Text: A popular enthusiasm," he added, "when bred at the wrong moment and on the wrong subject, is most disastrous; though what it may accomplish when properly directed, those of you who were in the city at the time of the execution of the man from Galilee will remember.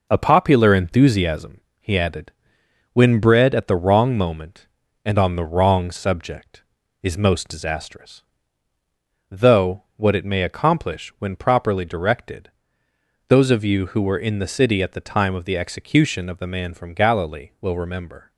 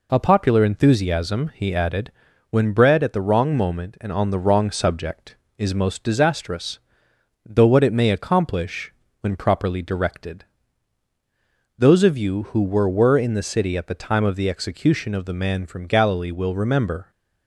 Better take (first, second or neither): first